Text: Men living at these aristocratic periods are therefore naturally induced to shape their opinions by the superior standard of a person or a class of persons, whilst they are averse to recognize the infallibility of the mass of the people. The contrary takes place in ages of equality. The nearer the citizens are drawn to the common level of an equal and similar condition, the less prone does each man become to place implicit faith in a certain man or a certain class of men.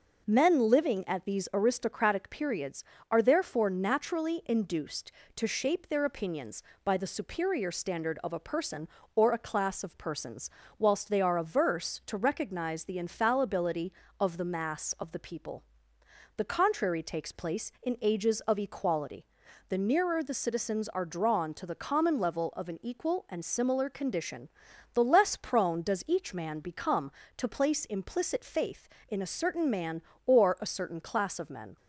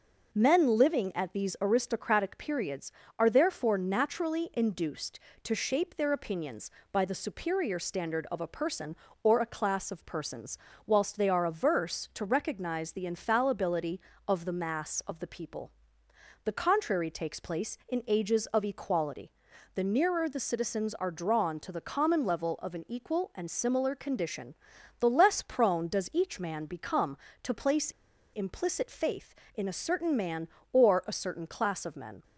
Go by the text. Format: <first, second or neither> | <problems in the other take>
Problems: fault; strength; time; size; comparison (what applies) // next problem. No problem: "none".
first | pauses between "place" and "implicit"; at 27.8 s; 0.43 s long